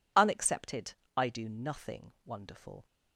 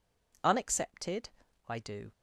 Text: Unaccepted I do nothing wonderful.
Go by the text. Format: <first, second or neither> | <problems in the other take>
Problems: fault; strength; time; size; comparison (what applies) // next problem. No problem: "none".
first | pauses between "Unaccepted" and "I"; at 1.2 s; 0.38 s long; slight in the first // stops before "nothing wonderful"; at 2.1 s